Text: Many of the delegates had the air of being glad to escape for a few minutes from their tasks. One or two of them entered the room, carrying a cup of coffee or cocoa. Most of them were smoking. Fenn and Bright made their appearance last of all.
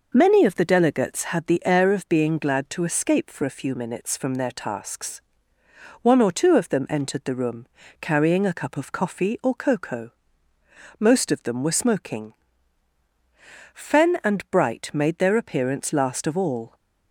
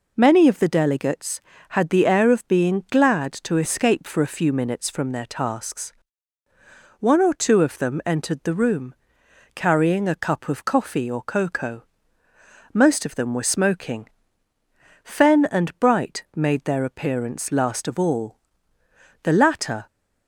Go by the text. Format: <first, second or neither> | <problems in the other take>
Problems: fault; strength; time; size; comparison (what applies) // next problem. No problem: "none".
first | goes on to say "The latter"; noticeable; from 19.2 s on; 0.64 s long